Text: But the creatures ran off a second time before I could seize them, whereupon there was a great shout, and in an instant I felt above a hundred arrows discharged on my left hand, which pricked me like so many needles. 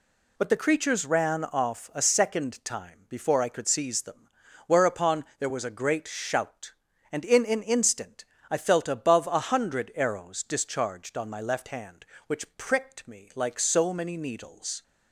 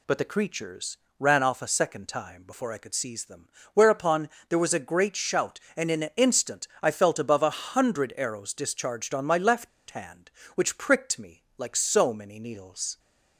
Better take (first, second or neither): first